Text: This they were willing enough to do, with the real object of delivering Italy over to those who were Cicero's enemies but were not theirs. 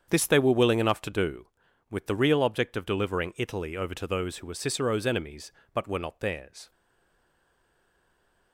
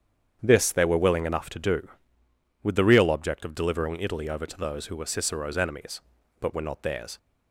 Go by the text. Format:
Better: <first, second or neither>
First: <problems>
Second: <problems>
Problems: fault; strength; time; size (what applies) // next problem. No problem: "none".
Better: second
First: starts louder than the rest; strong; until 1.1 s; 7.5 dB // stays silent after the last word; noticeable; from 6.7 s on; 1.8 s long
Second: starts louder than the rest; strong; until 1.4 s; 8.5 dB